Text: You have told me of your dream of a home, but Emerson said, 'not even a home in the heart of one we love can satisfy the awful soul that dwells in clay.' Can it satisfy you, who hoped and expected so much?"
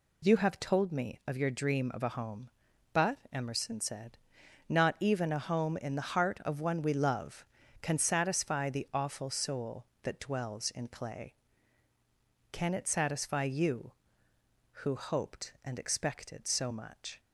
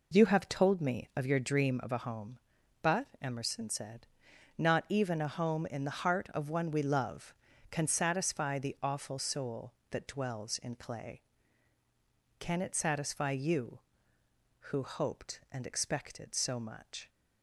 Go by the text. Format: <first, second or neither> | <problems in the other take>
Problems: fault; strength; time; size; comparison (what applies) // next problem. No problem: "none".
first | starts louder than the rest; noticeable; until 1.9 s; 4 dB // pauses between "but" and "Emerson"; slight; at 3.0 s; 0.16 s long; slight in the first